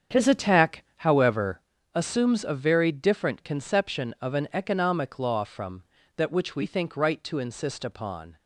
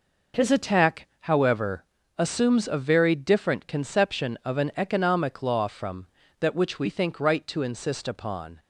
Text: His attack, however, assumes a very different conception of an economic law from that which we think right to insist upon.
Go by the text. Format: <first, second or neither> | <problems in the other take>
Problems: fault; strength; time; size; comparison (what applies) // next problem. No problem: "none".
second | starts louder than the rest; strong; until 1.7 s; 8 dB